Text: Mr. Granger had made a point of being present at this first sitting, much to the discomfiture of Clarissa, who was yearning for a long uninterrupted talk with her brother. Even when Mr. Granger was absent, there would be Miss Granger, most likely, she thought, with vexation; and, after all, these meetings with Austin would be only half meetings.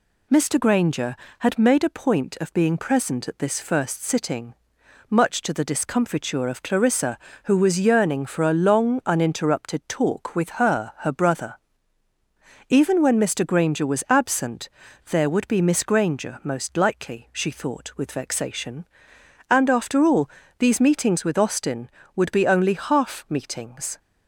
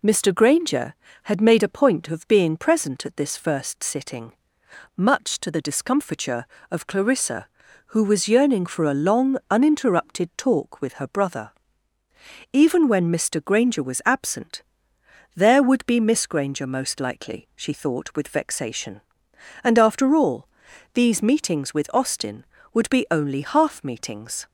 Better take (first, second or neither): second